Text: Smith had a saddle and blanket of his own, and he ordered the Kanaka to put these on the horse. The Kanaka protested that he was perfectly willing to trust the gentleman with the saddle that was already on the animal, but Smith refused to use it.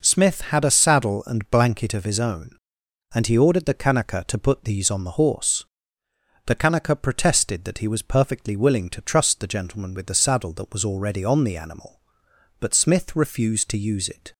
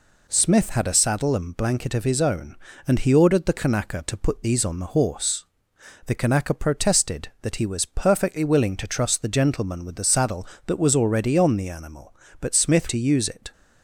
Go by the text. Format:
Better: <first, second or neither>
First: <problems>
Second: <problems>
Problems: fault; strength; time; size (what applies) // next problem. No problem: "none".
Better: first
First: none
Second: skips "refused"; at 12.8 s